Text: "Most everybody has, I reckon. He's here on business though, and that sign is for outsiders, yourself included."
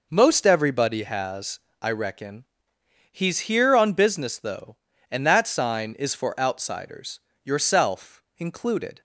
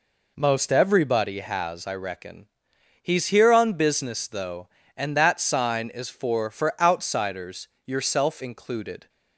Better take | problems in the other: first | says "for" twice; at 6.4 s

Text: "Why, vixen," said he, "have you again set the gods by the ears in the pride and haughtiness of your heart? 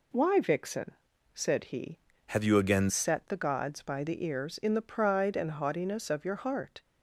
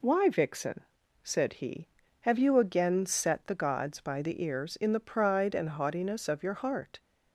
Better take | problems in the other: second | changes voice from "have" to "again"; from 2.2 to 2.9 s; 0.7 s long

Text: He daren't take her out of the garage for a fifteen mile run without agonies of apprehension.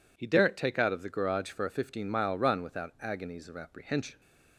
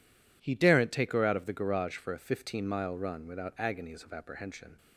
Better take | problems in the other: second | skips "her"; at 0.7 s

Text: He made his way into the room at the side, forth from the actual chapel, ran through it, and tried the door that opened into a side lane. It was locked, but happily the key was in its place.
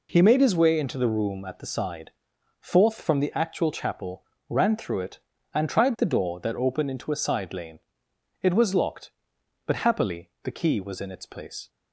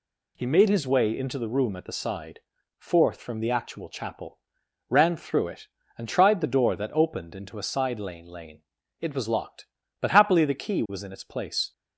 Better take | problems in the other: first | says "lane" twice; at 8.2 s

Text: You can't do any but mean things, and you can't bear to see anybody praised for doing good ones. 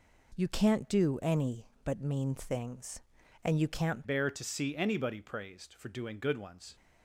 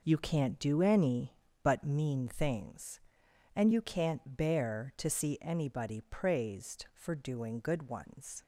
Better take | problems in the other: second | changes voice at "bear"; from 4.0 s on; 2.7 s long

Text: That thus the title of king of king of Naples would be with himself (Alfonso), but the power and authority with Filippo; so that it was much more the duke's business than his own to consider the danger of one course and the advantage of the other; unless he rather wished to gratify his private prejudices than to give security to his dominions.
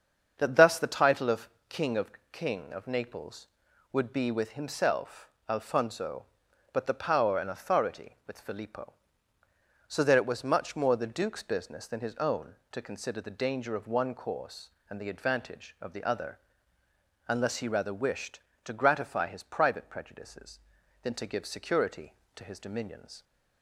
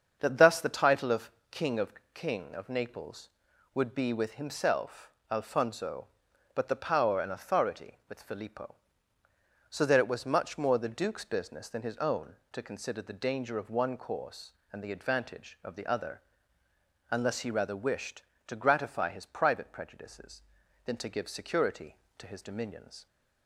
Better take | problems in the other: neither | starts louder than the rest; the same in both // pauses between "of" and "king"; slight; the same in both // pauses between "of" and "king"; slight; the same in both

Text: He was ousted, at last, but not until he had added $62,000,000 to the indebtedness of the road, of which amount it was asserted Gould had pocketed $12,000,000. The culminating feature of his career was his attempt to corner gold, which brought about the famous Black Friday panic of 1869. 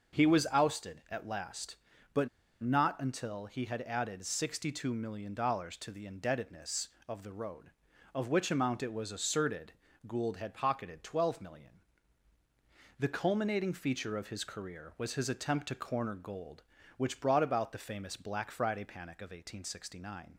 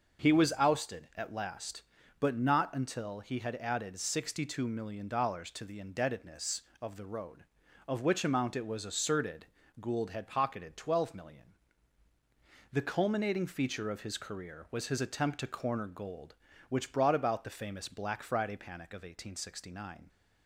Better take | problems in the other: second | starts louder than the rest; noticeable; until 1.2 s; 6 dB; noticeable in the second // pauses between "but" and "not"; slight; at 2.2 s; 0.33 s long // pauses between "asserted" and "Gould"; slight; at 9.7 s; 0.34 s long; slight in the second

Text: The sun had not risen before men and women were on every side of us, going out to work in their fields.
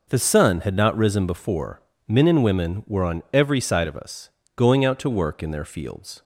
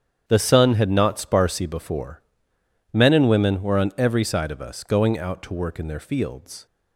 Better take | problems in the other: first | starts louder than the rest; strong; until 1.2 s; 8.5 dB // says "sparsy" for "risen"; at 1.2 s // pauses between "before" and "men"; noticeable; at 2.2 s; 0.72 s long; slight in the first

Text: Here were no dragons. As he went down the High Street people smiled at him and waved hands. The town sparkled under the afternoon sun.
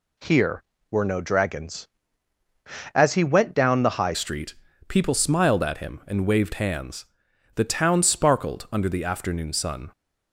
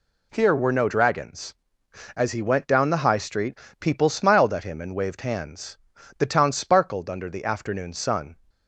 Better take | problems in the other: second | changes voice at "Street"; from 4.1 s on; 5.8 s long // pauses between "Street" and "people"; slight; at 4.5 s; 0.32 s long; slight in the second

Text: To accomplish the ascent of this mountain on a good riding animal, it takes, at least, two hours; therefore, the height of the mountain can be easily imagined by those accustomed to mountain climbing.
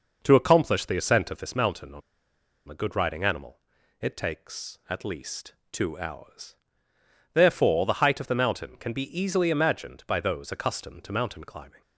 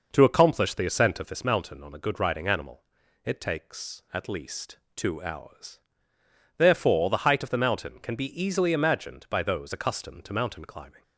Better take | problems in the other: second | pauses between "on" and "a"; noticeable; at 2.0 s; 0.67 s long

